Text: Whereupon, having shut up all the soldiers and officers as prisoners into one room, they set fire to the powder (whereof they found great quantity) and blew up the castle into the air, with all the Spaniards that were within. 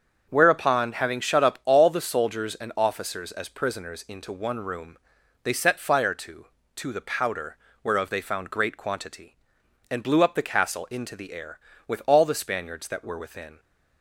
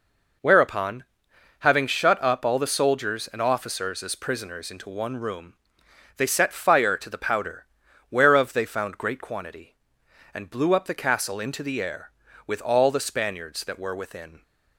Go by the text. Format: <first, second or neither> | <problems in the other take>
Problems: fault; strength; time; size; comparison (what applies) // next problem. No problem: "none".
second | starts louder than the rest; until 1.2 s; 7 dB // says "to" twice; at 6.7 s